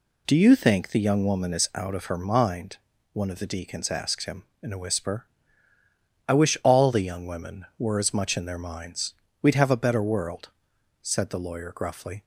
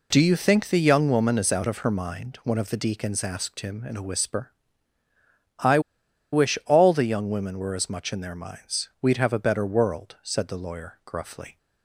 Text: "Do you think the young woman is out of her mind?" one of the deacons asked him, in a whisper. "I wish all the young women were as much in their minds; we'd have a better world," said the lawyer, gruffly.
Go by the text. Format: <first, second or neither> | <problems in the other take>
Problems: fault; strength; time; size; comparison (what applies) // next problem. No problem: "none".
first | pauses between "I" and "wish"; noticeable; at 5.7 s; 0.53 s long